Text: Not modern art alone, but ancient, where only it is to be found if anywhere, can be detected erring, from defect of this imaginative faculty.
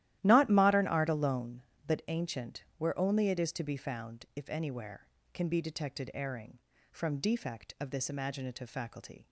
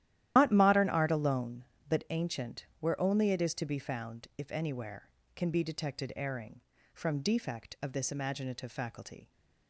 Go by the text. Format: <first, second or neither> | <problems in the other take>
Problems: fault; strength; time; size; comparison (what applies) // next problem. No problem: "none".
first | loses the start of "Not"; at 0.3 s; 125 ms // starts louder than the rest; strong; until 1.3 s; 13 dB; strong in the first